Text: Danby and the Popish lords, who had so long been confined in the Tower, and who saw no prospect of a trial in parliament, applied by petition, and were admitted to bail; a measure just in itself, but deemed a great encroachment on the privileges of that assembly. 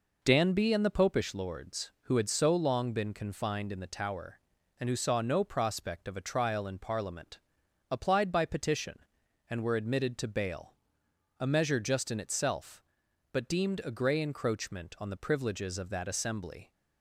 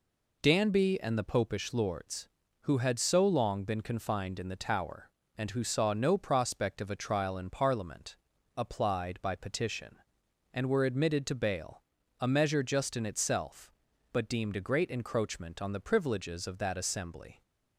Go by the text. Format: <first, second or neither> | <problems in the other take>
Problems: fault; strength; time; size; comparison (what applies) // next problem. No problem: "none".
second | says "grey" for "great"; at 13.9 s